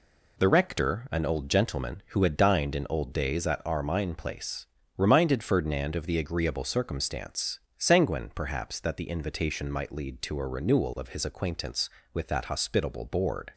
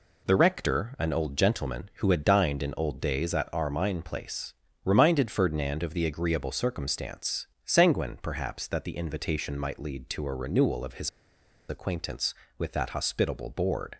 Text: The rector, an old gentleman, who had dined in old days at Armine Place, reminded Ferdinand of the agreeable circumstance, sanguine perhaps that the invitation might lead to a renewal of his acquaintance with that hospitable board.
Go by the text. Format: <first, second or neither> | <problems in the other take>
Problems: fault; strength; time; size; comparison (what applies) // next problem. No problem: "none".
first | pauses between "his" and "acquaintance"; noticeable; at 11.0 s; 0.59 s long